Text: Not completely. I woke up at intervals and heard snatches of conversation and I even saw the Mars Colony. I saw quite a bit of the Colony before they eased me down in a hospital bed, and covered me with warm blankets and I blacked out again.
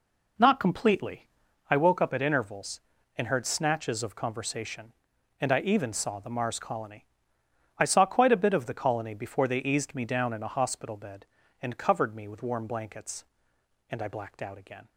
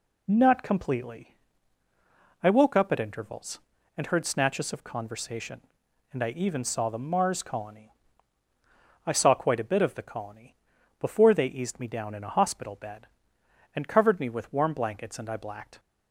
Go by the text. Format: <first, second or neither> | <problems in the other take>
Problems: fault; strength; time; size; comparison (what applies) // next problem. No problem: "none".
first | pauses between "Colony" and "before"; at 10.5 s; 0.44 s long // stops before "out again"; at 15.7 s